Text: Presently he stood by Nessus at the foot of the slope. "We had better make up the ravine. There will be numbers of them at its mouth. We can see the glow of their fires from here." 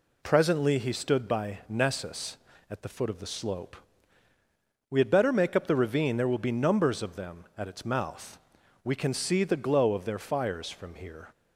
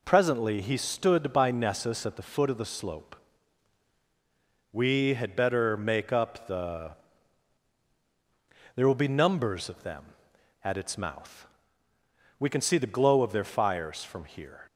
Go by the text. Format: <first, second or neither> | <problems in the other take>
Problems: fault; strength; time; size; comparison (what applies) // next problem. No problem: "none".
first | skips "ravine"; at 7.8 s